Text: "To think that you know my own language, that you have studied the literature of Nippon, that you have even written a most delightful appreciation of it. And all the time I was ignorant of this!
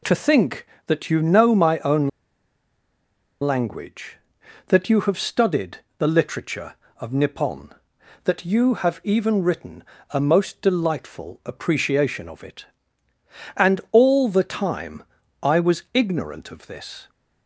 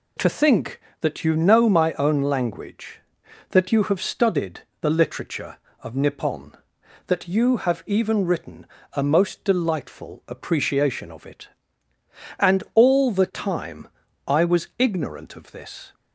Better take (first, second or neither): second